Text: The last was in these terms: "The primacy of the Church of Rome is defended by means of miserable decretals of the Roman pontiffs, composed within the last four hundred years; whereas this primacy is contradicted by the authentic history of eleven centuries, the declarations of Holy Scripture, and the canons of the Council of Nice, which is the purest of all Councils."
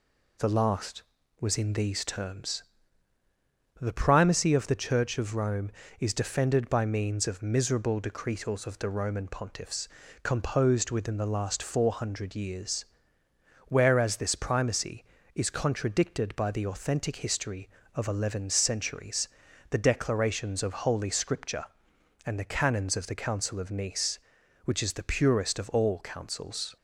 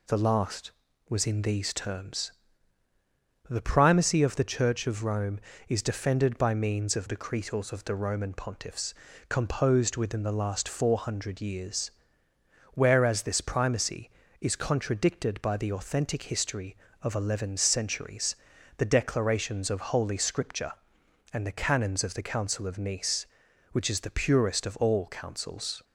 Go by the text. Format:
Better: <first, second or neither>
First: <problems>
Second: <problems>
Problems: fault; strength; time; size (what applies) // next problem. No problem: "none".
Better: first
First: none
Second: skips "miserable"; at 7.0 s